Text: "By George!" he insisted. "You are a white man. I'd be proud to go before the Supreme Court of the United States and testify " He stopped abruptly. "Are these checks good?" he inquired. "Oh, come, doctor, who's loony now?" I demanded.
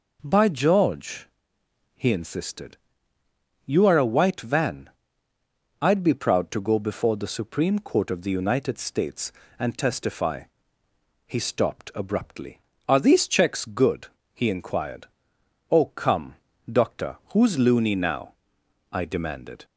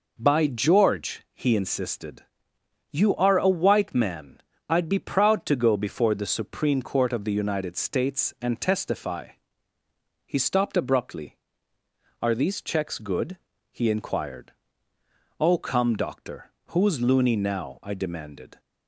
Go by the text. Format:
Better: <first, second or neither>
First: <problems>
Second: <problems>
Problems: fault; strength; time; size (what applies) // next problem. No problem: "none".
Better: second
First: says "van" for "man"; at 4.4 s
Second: none